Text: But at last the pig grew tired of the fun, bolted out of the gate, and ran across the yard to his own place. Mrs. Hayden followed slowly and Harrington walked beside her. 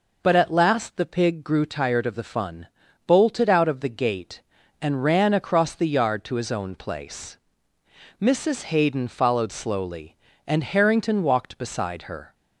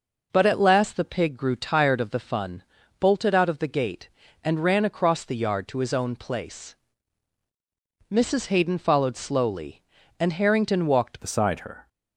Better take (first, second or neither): first